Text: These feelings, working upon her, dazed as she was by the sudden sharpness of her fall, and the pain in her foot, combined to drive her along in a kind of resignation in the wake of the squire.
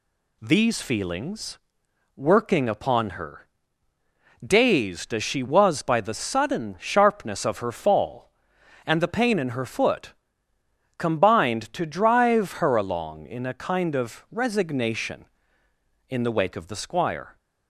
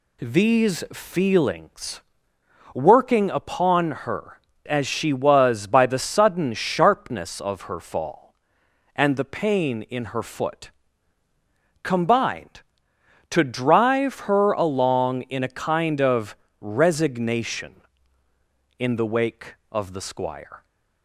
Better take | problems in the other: first | skips "dazed"; at 4.5 s // pauses between "of" and "resignation"; slight; at 16.3 s; 0.24 s long

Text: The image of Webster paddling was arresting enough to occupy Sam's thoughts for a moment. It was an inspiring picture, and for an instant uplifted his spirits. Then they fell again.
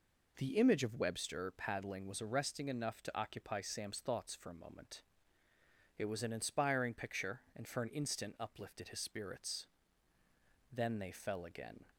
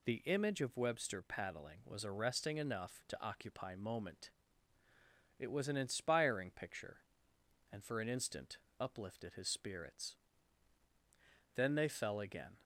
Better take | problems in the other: first | skips "Sam's thoughts for a"; at 3.7 s // pauses between "instant" and "uplifted"; slight; at 8.5 s; 0.22 s long

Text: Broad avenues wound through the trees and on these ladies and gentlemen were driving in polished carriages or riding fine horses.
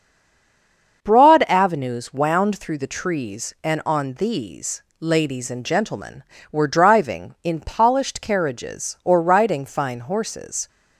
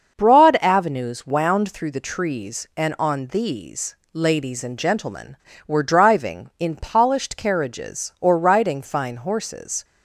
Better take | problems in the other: second | stays silent before the first word; until 1.0 s; 1.0 s long // starts louder than the rest; until 2.0 s; 6.5 dB; also in the second // pauses between "these" and "ladies"; slight; at 4.8 s; 0.18 s long; slight in the second

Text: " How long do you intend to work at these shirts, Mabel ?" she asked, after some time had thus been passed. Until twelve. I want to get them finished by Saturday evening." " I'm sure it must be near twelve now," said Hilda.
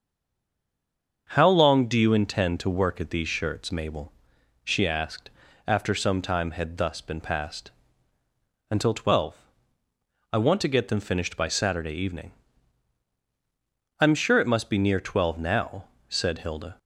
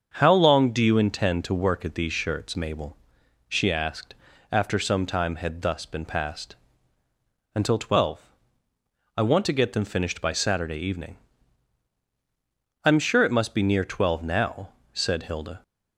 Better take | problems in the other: second | stays silent before the first word; noticeable; until 1.2 s; 1.2 s long // starts louder than the rest; until 2.3 s; 6.5 dB; also in the second

